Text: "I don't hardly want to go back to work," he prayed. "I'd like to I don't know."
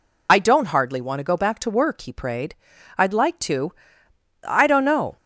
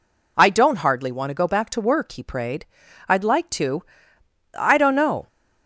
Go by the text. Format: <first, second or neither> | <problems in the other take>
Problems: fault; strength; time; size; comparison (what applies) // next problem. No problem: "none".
second | loses the start of "I"; at 0.2 s; 40 ms // pauses between "to" and "I"; noticeable; at 3.7 s; 0.72 s long; noticeable in the second